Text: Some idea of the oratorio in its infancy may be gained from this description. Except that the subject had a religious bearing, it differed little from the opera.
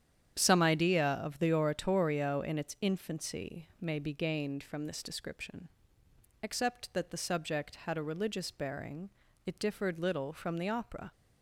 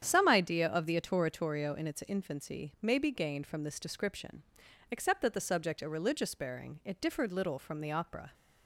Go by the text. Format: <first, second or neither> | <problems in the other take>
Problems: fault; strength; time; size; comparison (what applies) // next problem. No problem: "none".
first | starts louder than the rest; strong; until 1.1 s; 9 dB; strong in the first // skips "had"; at 5.8 s